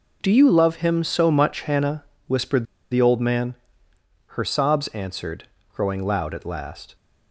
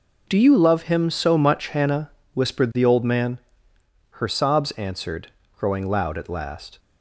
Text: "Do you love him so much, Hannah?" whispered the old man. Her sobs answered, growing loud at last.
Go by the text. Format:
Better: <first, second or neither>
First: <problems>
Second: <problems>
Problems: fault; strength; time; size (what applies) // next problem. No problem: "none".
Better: second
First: pauses between "whispered" and "the"; slight; at 2.6 s; 0.28 s long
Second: none